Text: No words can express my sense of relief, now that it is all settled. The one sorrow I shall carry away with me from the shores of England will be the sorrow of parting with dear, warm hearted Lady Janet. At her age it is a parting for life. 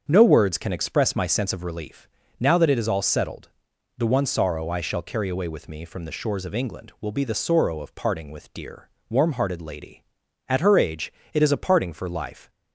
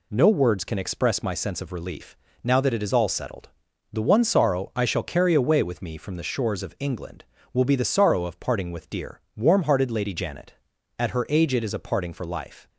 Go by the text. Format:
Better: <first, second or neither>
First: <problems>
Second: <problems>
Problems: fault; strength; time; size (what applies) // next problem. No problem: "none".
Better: second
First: starts louder than the rest; until 1.1 s; 7 dB // skips "Janet"; at 10.2 s // pauses between "age" and "it"; slight; at 11.1 s; 0.22 s long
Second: none